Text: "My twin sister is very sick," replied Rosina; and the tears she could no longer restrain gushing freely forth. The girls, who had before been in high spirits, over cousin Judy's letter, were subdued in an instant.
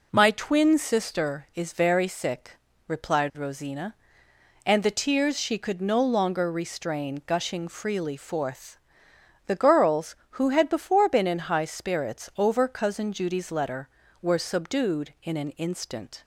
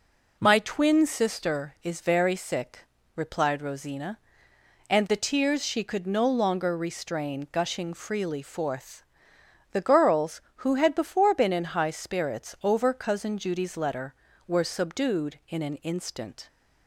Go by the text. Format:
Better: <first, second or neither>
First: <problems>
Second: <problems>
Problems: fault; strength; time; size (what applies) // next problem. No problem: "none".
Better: neither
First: none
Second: none